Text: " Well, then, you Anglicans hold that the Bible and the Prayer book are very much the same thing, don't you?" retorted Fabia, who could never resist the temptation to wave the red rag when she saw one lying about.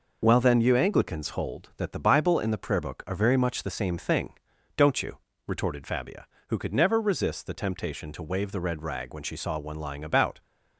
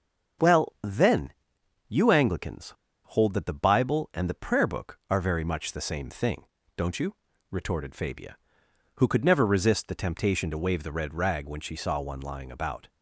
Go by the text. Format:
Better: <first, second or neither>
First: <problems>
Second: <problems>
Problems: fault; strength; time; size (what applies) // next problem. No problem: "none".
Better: first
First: none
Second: starts louder than the rest; noticeable; until 2.0 s; 6 dB // pauses between "Anglicans" and "hold"; slight; at 2.7 s; 0.34 s long